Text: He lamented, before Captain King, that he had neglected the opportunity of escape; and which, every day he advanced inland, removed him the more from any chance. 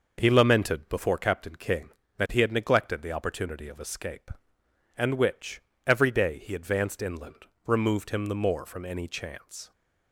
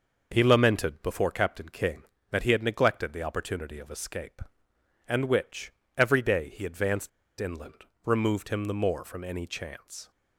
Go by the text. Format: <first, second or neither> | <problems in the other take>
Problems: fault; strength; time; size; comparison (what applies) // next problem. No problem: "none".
first | pauses between "advanced" and "inland"; slight; at 7.0 s; 0.30 s long